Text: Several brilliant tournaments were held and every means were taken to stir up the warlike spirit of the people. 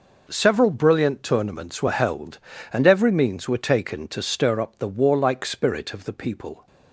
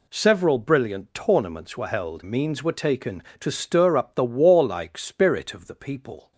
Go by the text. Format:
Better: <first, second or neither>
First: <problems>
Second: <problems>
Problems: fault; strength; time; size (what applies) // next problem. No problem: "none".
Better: first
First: none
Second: skips "and every"; at 2.2 s